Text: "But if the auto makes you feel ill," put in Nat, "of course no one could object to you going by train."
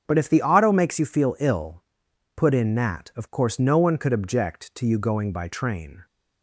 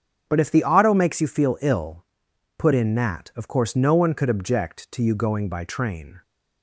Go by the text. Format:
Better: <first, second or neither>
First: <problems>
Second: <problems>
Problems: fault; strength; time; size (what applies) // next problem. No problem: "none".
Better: neither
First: starts louder than the rest; strong; until 1.0 s; 7.5 dB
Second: starts louder than the rest; strong; until 1.2 s; 8 dB